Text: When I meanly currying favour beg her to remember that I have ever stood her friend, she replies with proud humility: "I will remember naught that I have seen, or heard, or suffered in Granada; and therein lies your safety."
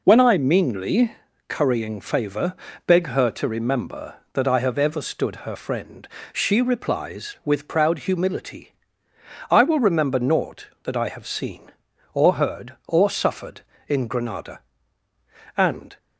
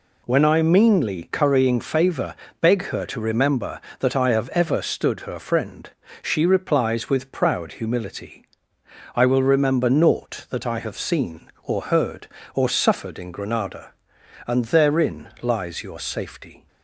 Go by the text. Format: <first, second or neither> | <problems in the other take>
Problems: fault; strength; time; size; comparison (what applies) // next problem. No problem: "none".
second | pauses between "meanly" and "currying"; slight; at 1.1 s; 0.36 s long // pauses between "favour" and "beg"; slight; at 2.5 s; 0.32 s long; slight in the second // stops before "therein lies your safety"; at 15.9 s